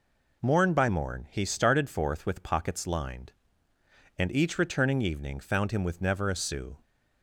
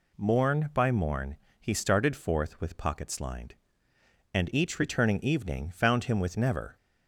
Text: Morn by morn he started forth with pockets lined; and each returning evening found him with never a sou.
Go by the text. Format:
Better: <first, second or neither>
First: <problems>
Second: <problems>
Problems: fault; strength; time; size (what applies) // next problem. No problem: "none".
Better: first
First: none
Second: pauses between "morn" and "he"; slight; at 1.3 s; 0.24 s long // stops before "a sou"; at 6.7 s